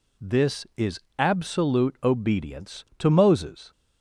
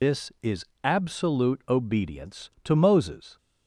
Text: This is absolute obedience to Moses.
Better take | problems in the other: first | loses the start of "This"; at 0.0 s; 170 ms // pauses between "is" and "absolute"; slight; at 0.6 s; 0.20 s long; slight in the first

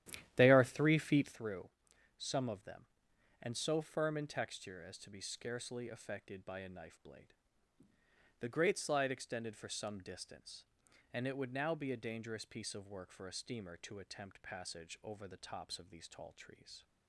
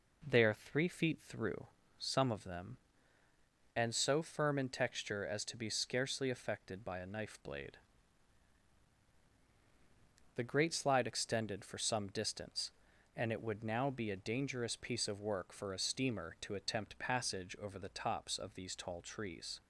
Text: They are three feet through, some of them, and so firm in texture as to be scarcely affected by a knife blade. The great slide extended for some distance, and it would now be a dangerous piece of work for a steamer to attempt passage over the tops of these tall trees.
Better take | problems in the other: second | starts louder than the rest; strong; until 1.5 s; 12 dB

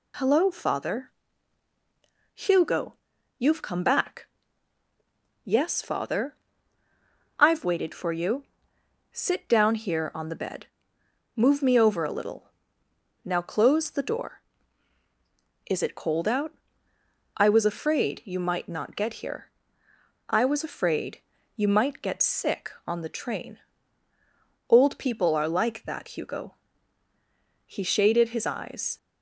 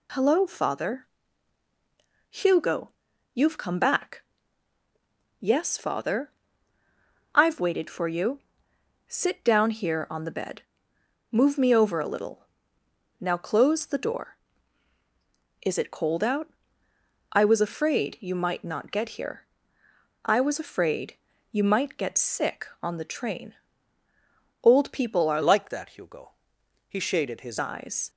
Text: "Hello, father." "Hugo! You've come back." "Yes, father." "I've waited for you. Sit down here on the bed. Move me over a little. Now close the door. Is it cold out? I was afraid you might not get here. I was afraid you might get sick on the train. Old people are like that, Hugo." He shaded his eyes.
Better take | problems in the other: first | pauses between "afraid" and "you"; at 21.1 s; 0.38 s long; also in the first // changes voice from "like" to "his"; from 25.4 to 27.5 s; 2.1 s long

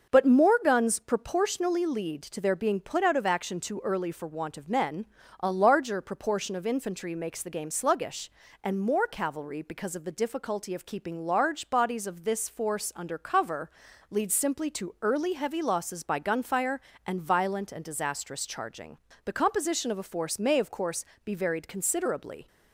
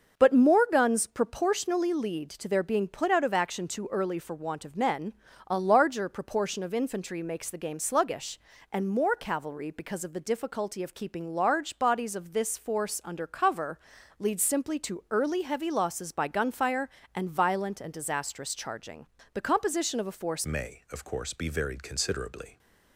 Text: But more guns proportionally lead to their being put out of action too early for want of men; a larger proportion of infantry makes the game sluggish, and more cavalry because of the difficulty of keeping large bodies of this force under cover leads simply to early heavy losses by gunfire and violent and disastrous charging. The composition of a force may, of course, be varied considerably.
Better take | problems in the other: first | starts louder than the rest; until 1.2 s; 6.5 dB; also in the first // pauses between "cover" and "leads"; at 13.7 s; 0.40 s long; also in the first // changes voice at "may"; from 20.4 s on; 2.1 s long

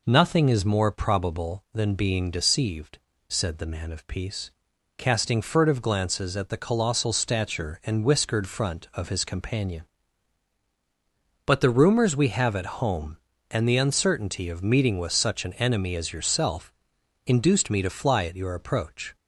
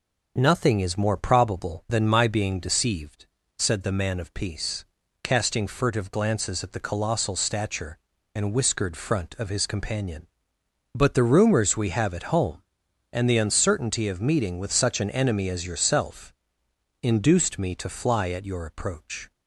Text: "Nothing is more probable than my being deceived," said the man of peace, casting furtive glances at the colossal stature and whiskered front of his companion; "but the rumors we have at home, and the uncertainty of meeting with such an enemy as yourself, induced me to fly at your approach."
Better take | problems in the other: second | skips "my"; at 1.9 s

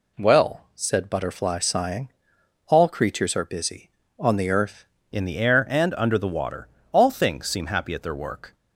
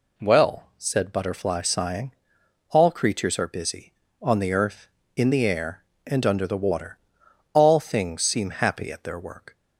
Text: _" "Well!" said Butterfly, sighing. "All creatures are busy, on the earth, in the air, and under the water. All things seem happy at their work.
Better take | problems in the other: second | changes voice at "in"; from 5.1 s on; 3.4 s long

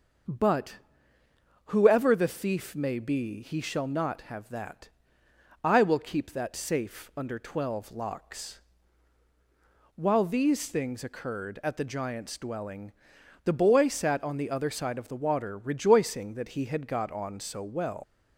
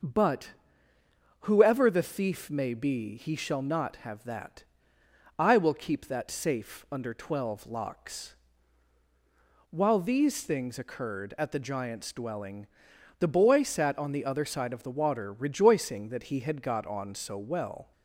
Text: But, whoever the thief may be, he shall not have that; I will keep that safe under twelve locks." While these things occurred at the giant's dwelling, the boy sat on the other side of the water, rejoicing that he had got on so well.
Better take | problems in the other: second | starts louder than the rest; until 2.1 s; 6 dB; also in the second // leaves "well" unfinished; at 18.0 s; 130 ms

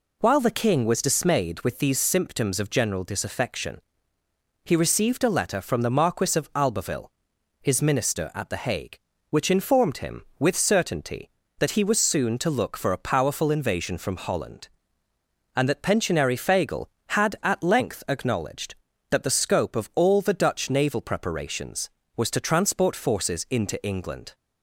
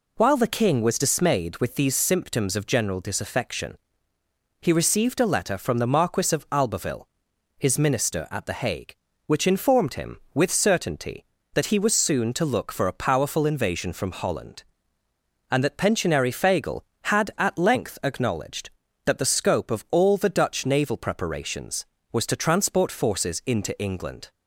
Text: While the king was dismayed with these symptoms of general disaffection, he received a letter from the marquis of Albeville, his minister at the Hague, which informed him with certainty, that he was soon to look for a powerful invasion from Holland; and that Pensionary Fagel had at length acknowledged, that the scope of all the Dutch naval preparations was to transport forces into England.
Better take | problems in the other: neither | none

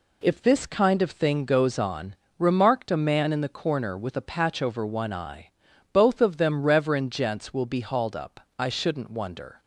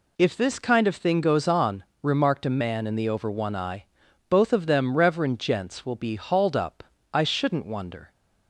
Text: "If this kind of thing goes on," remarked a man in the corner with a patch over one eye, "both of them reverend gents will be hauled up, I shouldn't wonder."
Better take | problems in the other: first | skips "corner with a patch"; at 3.0 s

